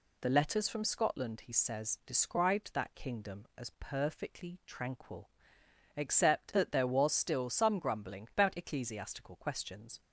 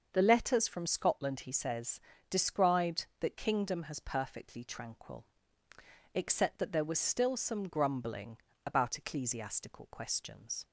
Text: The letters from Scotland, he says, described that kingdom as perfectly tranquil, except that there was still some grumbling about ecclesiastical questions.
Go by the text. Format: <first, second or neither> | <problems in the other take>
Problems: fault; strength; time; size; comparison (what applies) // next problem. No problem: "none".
first | starts louder than the rest; until 1.1 s; 6.5 dB // says "has" for "as"; at 3.8 s // pauses between "grumbling" and "about"; slight; at 8.3 s; 0.28 s long